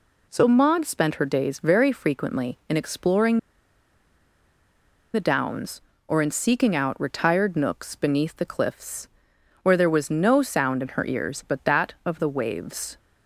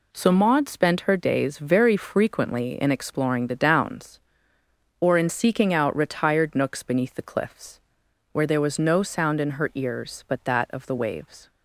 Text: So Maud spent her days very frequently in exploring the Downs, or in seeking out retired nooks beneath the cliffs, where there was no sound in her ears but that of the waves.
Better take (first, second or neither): second